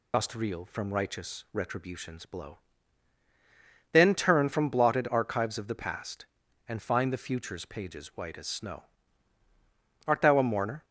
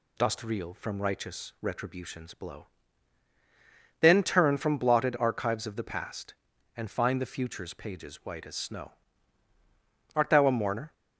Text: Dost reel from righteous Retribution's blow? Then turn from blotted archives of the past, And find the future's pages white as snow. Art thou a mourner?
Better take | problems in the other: second | loses the start of "Dost"; at 0.1 s; 35 ms

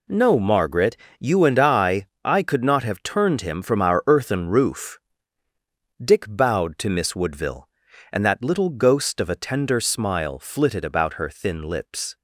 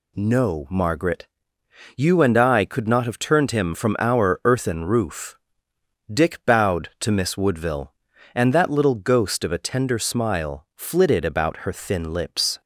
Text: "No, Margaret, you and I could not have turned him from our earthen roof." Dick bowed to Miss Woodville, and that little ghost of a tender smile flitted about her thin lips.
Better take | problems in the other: second | says "I" twice; at 2.2 s

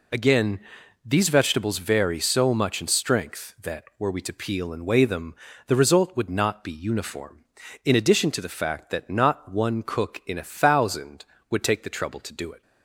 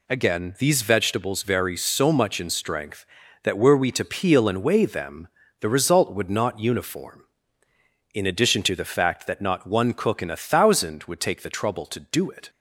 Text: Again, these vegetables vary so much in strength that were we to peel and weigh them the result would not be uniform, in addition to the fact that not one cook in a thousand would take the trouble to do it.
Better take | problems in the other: first | pauses between "them" and "the"; slight; at 5.2 s; 0.32 s long; slight in the first // skips "be"; at 6.5 s

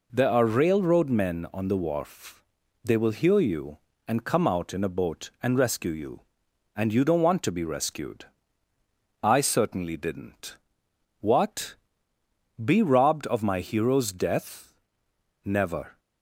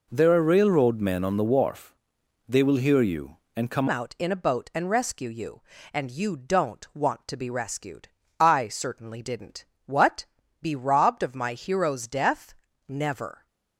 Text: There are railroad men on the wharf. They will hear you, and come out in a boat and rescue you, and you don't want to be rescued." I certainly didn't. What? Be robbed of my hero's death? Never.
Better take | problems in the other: first | changes voice at "out"; from 3.8 s on; 9.6 s long

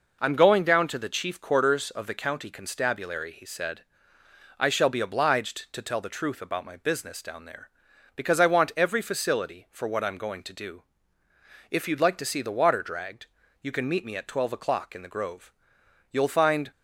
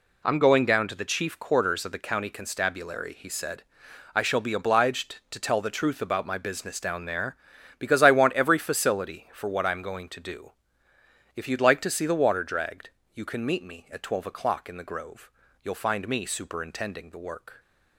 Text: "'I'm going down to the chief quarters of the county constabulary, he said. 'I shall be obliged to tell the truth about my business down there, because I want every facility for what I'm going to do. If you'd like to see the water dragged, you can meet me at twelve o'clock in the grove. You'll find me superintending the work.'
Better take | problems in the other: second | stops before "me superintending the work"; at 16.7 s

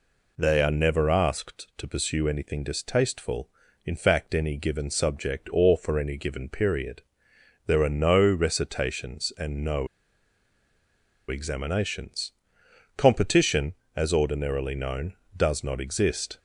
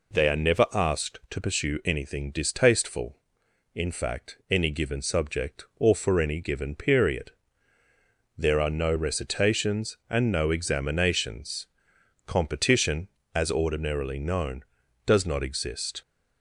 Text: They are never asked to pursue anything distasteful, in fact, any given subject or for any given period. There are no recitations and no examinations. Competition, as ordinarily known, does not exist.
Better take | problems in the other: second | pauses between "no" and "examinations"; strong; at 9.8 s; 1.4 s long

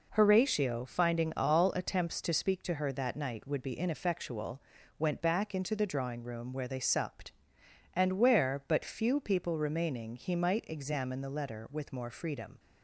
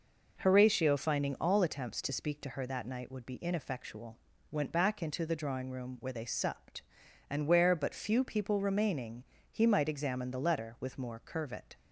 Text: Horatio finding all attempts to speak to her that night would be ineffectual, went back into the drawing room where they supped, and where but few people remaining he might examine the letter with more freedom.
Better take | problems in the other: first | pauses between "remaining" and "he"; slight; at 9.2 s; 0.28 s long // says "curvet" for "freedom"; at 11.2 s

